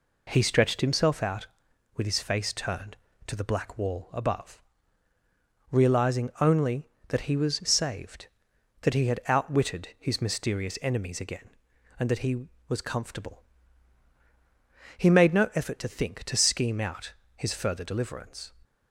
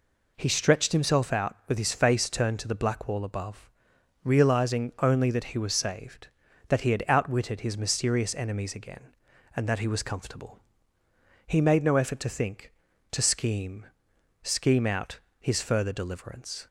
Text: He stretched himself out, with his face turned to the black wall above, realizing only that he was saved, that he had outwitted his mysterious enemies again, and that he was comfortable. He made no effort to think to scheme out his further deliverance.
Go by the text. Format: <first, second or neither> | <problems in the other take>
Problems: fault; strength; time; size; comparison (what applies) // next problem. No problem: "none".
first | says "scheme" twice; at 14.4 s // pauses between "out" and "his"; slight; at 15.1 s; 0.20 s long; slight in the first